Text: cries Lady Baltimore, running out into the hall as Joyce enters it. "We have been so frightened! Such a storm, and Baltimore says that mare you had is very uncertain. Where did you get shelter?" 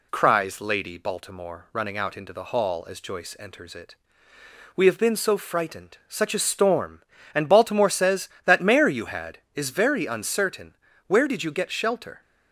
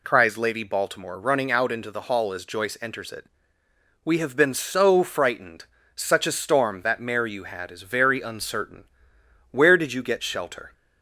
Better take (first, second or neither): first